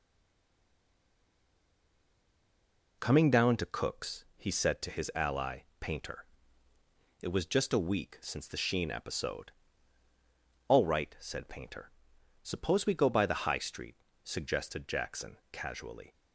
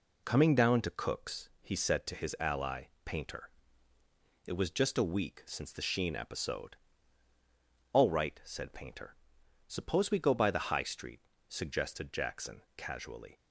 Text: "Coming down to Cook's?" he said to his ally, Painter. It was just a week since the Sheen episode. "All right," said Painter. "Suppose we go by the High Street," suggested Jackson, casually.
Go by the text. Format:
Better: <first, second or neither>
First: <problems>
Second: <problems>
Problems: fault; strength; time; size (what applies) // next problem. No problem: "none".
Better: second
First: stays silent before the first word; strong; until 3.0 s; 3.0 s long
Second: none